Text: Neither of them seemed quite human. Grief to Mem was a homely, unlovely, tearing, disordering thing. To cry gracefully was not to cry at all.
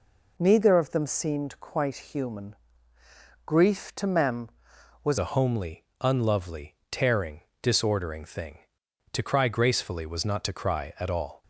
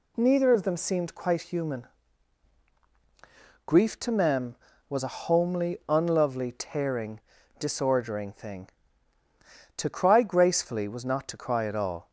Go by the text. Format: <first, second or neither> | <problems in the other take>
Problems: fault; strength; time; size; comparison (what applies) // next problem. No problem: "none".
second | changes voice at "a"; from 5.1 s on; 6.3 s long